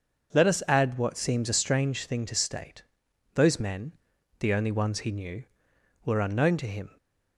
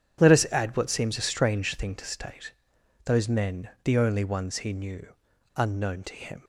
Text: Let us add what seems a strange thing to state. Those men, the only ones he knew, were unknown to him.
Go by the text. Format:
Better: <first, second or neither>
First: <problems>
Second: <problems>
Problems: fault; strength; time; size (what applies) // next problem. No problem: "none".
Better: first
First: none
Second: skips "were"; at 5.3 s